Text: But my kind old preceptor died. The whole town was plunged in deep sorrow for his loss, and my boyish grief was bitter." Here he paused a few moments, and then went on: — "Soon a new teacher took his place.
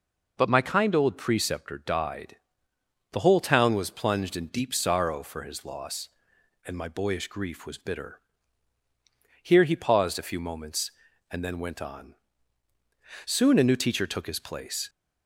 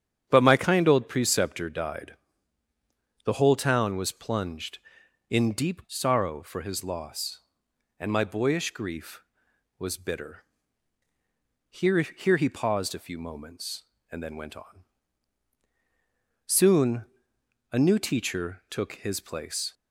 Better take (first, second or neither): first